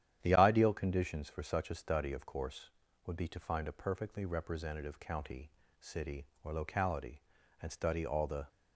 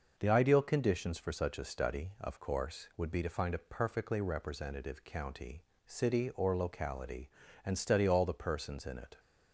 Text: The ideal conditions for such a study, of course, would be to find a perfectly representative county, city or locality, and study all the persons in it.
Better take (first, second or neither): second